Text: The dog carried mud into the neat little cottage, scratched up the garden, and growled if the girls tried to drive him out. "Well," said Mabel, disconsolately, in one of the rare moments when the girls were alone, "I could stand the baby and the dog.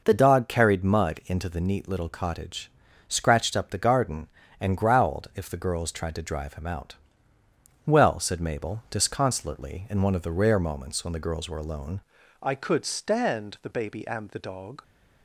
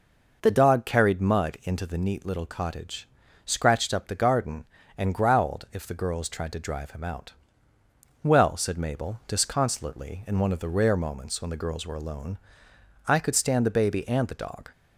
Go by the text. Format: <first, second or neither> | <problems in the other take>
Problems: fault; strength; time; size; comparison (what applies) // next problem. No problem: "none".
second | changes voice at "I"; from 12.4 s on; 2.4 s long